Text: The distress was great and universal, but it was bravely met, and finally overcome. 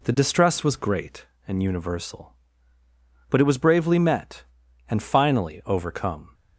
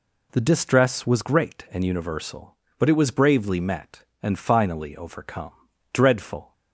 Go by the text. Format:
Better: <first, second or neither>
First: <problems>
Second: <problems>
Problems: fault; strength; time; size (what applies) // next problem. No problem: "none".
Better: first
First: none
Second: goes on to say "Dreadful"; from 5.9 s on; 0.60 s long